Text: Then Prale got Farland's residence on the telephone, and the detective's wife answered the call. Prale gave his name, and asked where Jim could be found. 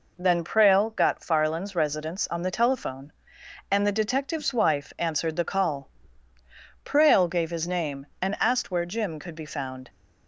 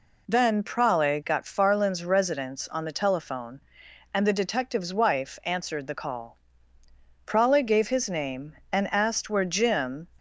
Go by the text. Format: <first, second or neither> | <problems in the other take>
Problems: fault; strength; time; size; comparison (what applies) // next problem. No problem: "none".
first | stops before "could be found"; at 10.1 s